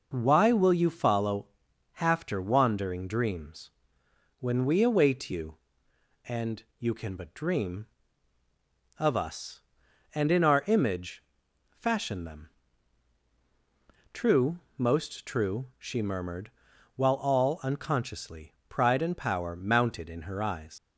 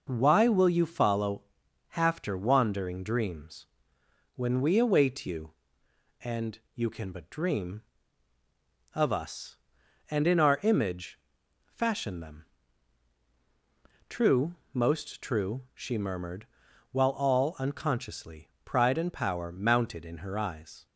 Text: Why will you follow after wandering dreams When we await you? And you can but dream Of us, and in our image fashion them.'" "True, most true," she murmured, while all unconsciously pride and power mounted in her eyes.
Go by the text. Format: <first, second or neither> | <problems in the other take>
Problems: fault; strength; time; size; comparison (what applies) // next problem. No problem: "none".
second | pauses between "follow" and "after"; noticeable; at 1.4 s; 0.52 s long; noticeable in the second // pauses between "dreams" and "When"; noticeable; at 3.7 s; 0.70 s long; noticeable in the second // pauses between "image" and "fashion"; noticeable; at 11.2 s; 0.46 s long; noticeable in the second // pauses between "unconsciously" and "pride"; slight; at 18.5 s; 0.16 s long; slight in the second // leaves "eyes" unfinished; at 20.7 s; 120 ms